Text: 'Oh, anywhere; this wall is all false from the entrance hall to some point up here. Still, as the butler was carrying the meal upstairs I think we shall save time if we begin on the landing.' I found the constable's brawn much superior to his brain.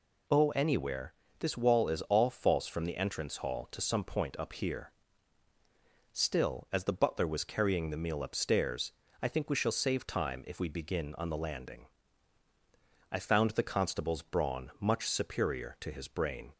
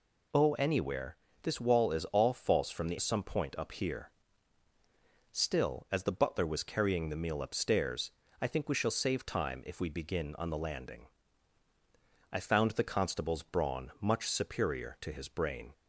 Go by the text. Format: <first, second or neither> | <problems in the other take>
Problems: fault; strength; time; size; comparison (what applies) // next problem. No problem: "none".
first | skips "entrance hall to"; at 2.9 s // pauses between "upstairs" and "I"; slight; at 8.1 s; 0.28 s long; slight in the first